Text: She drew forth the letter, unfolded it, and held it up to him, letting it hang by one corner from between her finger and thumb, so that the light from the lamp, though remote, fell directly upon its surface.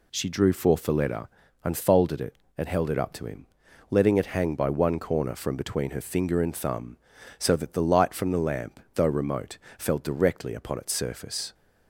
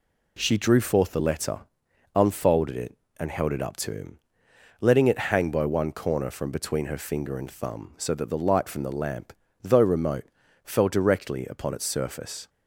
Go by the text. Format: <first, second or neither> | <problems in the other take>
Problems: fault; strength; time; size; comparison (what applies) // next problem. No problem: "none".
neither | none